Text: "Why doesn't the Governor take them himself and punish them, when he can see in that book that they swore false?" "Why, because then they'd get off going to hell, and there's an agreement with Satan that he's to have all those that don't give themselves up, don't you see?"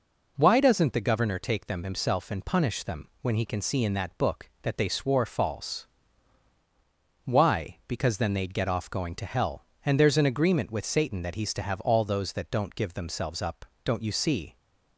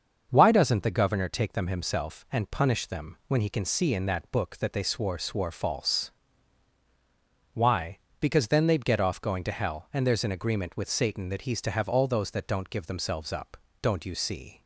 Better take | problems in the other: first | starts louder than the rest; until 1.3 s; 6.5 dB // says "swore" twice; at 5.1 s

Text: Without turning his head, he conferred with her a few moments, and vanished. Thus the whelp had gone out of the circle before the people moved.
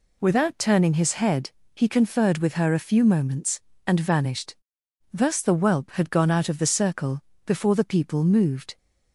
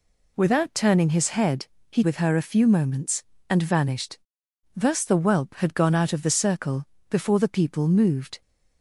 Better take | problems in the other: first | skips "conferred"; at 2.0 s // pauses between "circle" and "before"; slight; at 6.8 s; 0.24 s long; slight in the first

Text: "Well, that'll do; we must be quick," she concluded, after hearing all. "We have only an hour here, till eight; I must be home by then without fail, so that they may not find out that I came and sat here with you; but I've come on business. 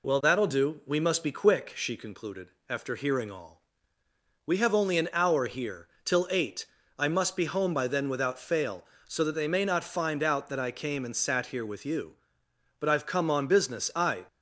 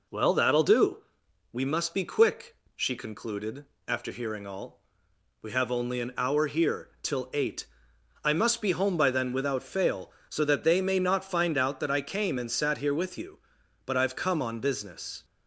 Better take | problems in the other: second | goes on to say "I"; slight; from 13.9 s on; 0.30 s long

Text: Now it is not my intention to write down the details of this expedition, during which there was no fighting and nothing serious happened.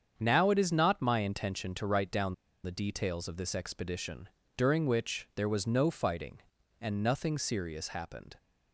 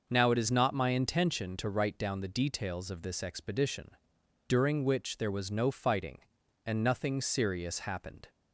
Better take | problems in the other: second | starts louder than the rest; strong; until 1.1 s; 7.5 dB // pauses between "down" and "the"; slight; at 2.3 s; 0.29 s long

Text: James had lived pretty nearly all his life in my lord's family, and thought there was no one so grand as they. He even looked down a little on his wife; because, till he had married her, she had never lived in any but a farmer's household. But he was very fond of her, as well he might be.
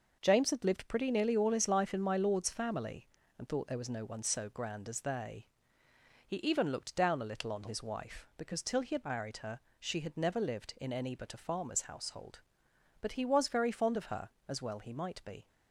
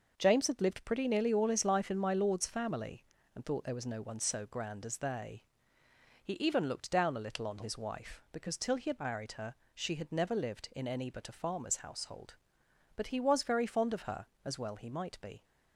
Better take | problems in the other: neither | none

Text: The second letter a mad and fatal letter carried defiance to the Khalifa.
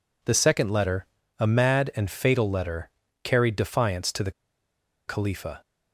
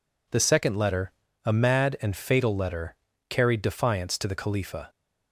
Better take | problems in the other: second | pauses between "letter" and "a"; slight; at 1.0 s; 0.34 s long; slight in the second // pauses between "letter" and "carried"; slight; at 2.8 s; 0.34 s long; slight in the second // pauses between "the" and "Khalifa"; noticeable; at 4.2 s; 0.77 s long

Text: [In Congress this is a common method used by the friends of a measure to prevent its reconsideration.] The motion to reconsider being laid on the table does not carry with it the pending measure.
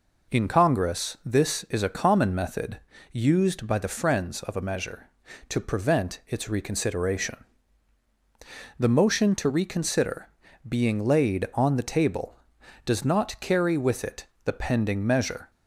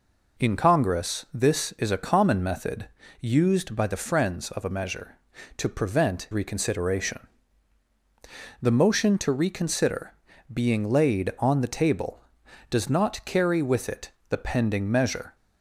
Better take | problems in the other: first | pauses between "method" and "used"; slight; at 2.8 s; 0.32 s long; slight in the first // skips "its"; at 6.3 s // pauses between "reconsider" and "being"; at 10.1 s; 0.38 s long; also in the first // pauses between "it" and "the"; slight; at 14.1 s; 0.16 s long; slight in the first

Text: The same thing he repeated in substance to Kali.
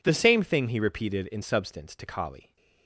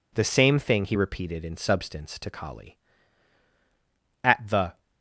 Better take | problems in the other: first | goes on to say "At the"; from 4.2 s on; 0.58 s long

